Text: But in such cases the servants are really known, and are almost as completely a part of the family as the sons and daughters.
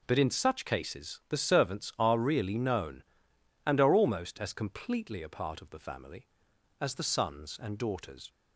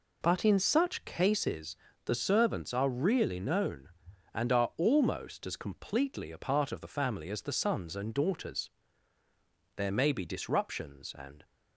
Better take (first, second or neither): first